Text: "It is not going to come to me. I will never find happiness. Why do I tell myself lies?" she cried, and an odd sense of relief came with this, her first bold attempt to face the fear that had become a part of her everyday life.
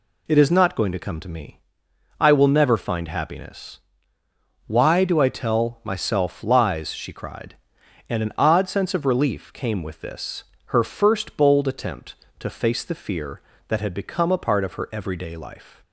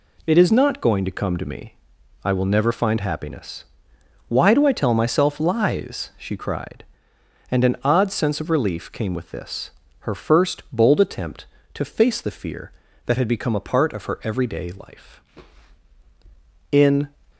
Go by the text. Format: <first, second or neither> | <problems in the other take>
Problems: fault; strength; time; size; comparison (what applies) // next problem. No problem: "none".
first | goes on to say "In"; slight; from 16.7 s on; 0.34 s long